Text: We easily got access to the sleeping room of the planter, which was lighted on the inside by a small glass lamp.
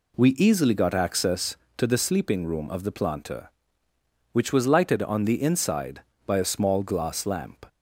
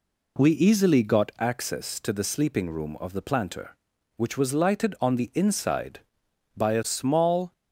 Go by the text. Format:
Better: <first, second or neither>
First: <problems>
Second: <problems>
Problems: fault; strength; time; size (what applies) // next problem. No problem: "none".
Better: first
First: none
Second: stops before "glass lamp"; at 7.5 s